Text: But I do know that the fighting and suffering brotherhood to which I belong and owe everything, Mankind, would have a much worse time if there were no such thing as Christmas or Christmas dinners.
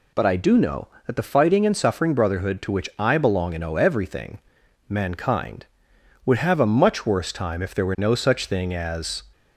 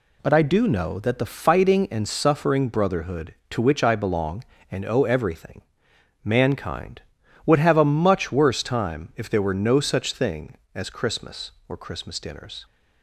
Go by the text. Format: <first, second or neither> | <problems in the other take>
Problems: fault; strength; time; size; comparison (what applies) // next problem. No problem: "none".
second | stops before "Christmas or Christmas dinners"; at 9.3 s